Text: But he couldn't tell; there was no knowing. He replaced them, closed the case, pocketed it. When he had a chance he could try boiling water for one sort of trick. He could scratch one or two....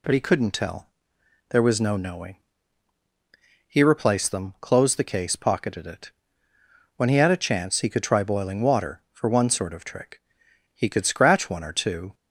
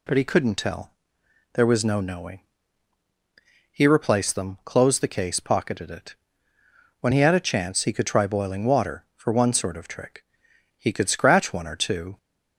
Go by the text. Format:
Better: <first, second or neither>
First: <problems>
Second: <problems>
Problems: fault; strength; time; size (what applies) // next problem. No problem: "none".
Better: neither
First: none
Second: none